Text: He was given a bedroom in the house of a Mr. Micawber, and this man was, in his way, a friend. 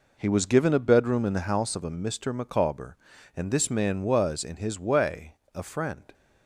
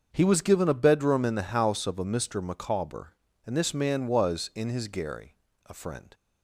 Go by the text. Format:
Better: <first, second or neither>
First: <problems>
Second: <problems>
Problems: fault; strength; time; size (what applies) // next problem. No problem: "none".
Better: first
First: none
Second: starts louder than the rest; until 1.1 s; 6.5 dB // says "gary" for "way"; at 4.8 s